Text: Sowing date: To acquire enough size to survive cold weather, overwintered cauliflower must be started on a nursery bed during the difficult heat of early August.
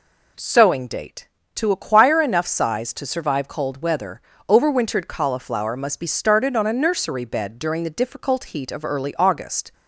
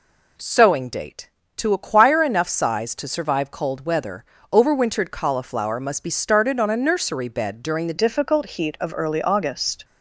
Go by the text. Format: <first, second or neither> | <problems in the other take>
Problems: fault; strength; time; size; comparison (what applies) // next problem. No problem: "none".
first | changes voice at "difficult"; from 7.9 s on; 1.9 s long